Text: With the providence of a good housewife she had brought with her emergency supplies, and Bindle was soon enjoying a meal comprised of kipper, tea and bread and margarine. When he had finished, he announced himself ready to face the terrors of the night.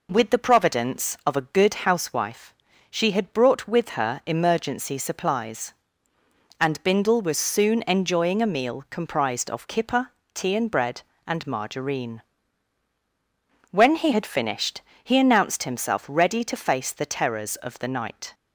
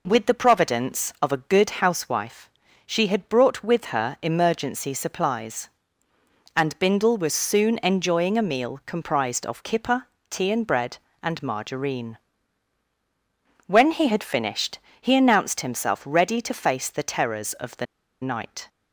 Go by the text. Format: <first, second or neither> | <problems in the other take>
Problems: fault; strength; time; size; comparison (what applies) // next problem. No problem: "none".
first | pauses between "housewife" and "she"; at 2.4 s; 0.38 s long; also in the first // pauses between "the" and "night"; at 17.8 s; 0.36 s long